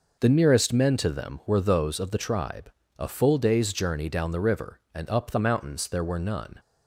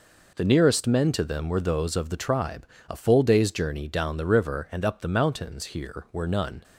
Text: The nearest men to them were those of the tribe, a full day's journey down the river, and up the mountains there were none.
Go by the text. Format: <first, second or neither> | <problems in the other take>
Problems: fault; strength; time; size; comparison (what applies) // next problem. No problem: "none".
first | says "here" for "there"; at 5.6 s